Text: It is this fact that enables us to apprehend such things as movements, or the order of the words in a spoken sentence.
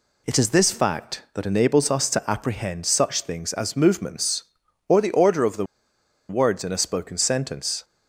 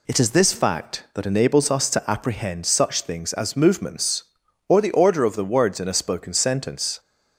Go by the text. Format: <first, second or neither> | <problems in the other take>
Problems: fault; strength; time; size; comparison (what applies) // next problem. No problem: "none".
second | pauses between "the" and "words"; noticeable; at 5.6 s; 0.63 s long